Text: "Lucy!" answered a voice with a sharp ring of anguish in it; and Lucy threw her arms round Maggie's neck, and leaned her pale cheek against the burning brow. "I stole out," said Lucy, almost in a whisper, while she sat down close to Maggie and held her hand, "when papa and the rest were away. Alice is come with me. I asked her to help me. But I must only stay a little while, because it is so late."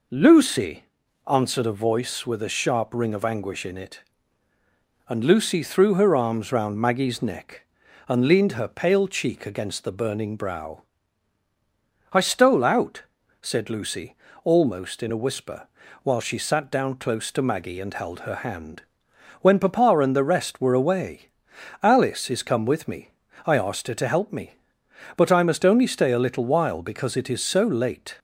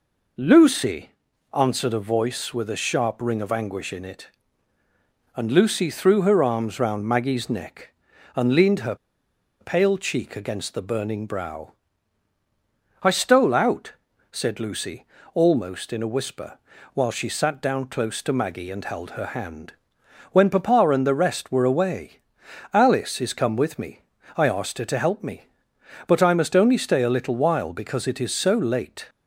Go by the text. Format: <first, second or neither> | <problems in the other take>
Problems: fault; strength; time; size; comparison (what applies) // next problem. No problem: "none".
first | pauses between "her" and "pale"; noticeable; at 8.9 s; 0.65 s long